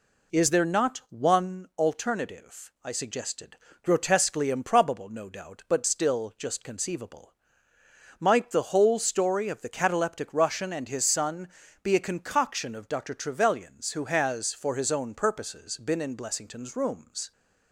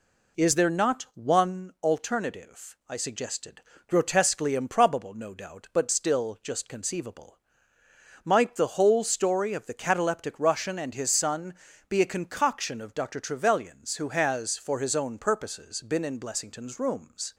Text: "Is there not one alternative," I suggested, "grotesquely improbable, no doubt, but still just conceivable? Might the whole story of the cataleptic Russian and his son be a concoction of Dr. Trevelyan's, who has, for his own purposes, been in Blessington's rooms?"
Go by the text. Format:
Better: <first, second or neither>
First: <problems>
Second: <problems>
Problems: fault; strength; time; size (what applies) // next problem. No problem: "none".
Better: neither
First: pauses between "son" and "be"; slight; at 11.4 s; 0.34 s long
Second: pauses between "son" and "be"; slight; at 11.5 s; 0.34 s long